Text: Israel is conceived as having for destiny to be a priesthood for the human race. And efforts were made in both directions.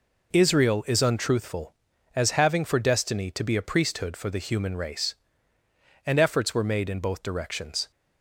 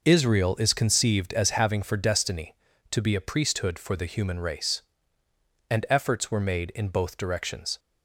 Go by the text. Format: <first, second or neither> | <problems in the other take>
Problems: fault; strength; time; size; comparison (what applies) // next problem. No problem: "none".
second | says "untruthful" for "conceived"; at 1.0 s